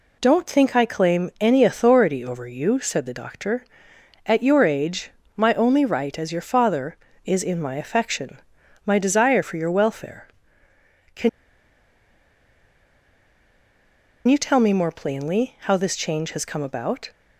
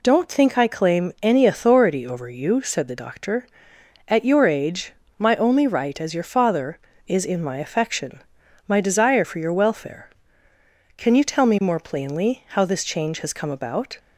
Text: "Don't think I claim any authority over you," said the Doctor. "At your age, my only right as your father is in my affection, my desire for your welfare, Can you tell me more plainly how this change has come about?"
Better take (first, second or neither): second